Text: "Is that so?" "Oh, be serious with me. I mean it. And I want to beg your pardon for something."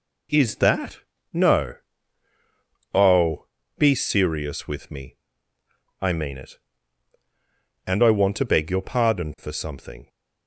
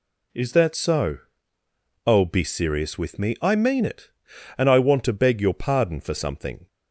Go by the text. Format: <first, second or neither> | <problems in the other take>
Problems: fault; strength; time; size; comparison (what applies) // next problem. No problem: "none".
second | says "no" for "so"; at 1.3 s